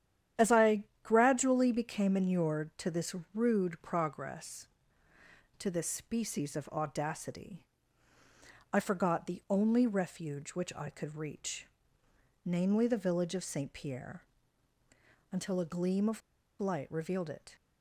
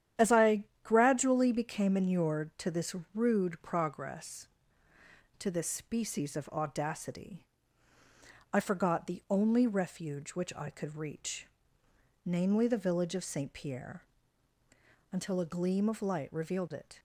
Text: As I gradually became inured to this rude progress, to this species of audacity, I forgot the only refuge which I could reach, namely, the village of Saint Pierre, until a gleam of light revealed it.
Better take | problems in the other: second | starts louder than the rest; strong; until 1.5 s; 10 dB; strong in the second // pauses between "I" and "gradually"; slight; at 0.8 s; 0.18 s long; slight in the second // pauses between "this" and "rude"; slight; at 3.1 s; 0.20 s long; slight in the second // pauses between "of" and "light"; at 16.2 s; 0.40 s long

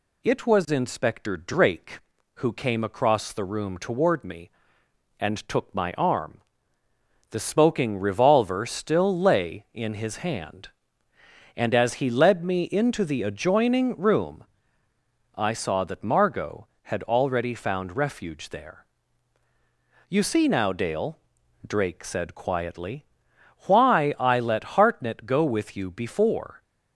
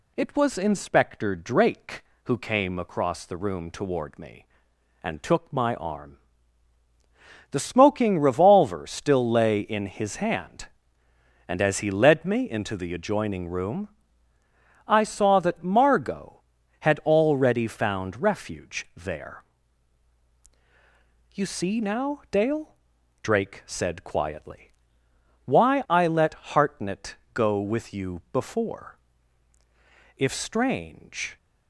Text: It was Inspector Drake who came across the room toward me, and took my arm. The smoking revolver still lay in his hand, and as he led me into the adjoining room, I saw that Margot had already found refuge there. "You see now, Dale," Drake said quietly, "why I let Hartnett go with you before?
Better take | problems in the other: first | pauses between "Hartnett" and "go"; slight; at 27.1 s; 0.18 s long // goes on to say "If Strange"; noticeable; from 30.1 s on; 1.2 s long

